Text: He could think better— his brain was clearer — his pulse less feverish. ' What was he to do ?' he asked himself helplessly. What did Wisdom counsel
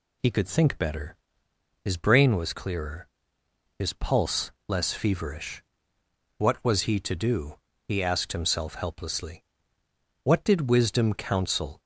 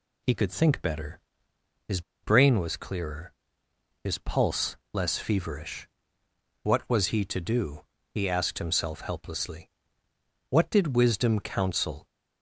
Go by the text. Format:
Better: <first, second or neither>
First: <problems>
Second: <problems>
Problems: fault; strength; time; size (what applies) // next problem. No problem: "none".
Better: first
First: pauses between "pulse" and "less"; slight; at 4.5 s; 0.16 s long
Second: pauses between "his" and "brain"; slight; at 2.0 s; 0.22 s long // pauses between "pulse" and "less"; slight; at 4.7 s; 0.16 s long